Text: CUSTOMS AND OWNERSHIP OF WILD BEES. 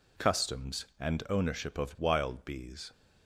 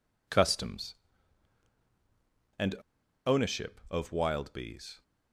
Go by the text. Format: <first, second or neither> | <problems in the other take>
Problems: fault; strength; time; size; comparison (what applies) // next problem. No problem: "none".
first | pauses between "AND" and "OWNERSHIP"; noticeable; at 2.7 s; 0.52 s long